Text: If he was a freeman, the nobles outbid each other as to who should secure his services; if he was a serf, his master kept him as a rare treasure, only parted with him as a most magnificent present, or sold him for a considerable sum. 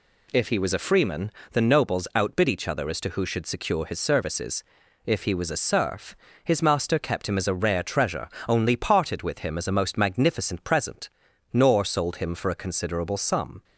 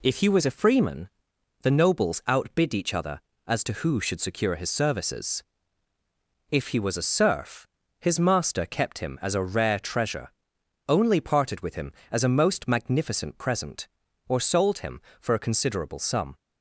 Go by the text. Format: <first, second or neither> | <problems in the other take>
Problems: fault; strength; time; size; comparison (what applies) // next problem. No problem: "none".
second | says "nor" for "or"; at 11.5 s